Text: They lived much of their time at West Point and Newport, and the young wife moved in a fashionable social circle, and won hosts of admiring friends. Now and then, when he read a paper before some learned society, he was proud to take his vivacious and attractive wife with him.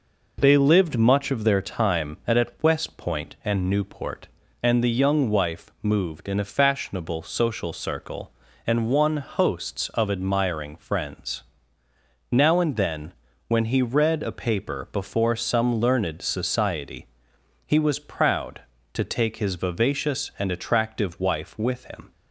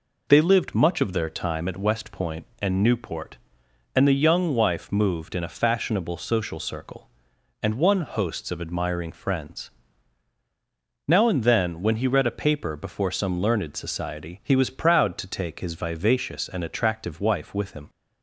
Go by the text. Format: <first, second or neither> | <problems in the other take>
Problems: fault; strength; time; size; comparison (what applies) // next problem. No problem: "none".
second | says "at" twice; at 2.3 s